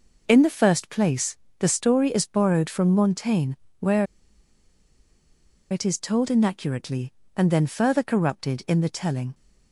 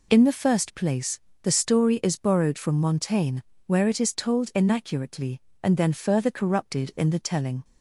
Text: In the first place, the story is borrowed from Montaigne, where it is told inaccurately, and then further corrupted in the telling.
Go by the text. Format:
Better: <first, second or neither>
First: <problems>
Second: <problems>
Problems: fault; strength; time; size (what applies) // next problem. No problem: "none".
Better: second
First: pauses between "where" and "it"; strong; at 4.0 s; 1.6 s long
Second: none